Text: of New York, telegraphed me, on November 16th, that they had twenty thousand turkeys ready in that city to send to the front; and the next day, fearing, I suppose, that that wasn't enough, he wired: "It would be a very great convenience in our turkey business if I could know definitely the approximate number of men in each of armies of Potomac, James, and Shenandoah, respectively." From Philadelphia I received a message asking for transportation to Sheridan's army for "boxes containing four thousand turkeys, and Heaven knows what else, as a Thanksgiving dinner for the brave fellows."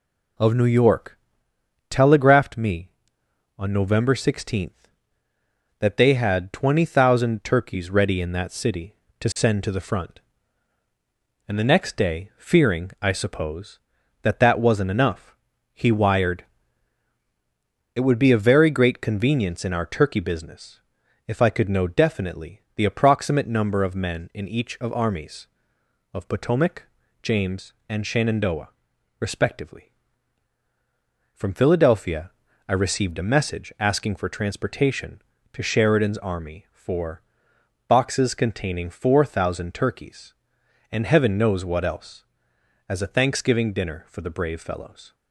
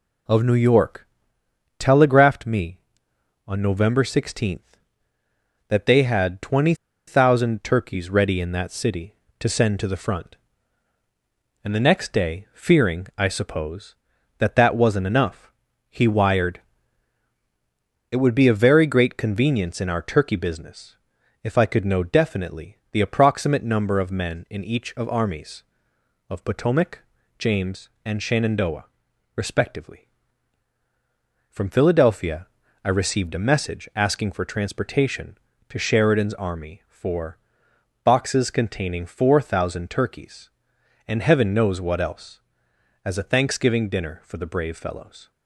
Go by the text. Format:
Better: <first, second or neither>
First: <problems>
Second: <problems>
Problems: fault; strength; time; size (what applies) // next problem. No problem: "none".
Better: first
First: pauses between "business" and "if"; noticeable; at 20.8 s; 0.46 s long // pauses between "Philadelphia" and "I"; at 32.3 s; 0.38 s long // pauses between "for" and "boxes"; noticeable; at 37.2 s; 0.66 s long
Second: pauses between "twenty" and "thousand"; slight; at 6.7 s; 0.33 s long // pauses between "business" and "if"; noticeable; at 20.9 s; 0.46 s long // pauses between "Philadelphia" and "I"; at 32.4 s; 0.38 s long // pauses between "for" and "boxes"; noticeable; at 37.3 s; 0.66 s long